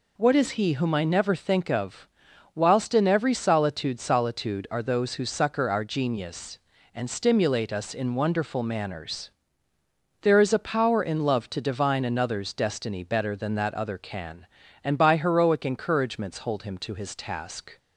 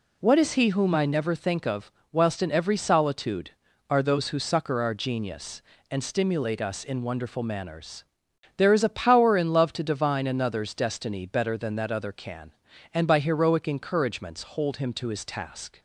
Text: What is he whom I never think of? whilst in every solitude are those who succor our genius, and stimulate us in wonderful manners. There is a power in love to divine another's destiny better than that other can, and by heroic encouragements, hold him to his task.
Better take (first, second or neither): second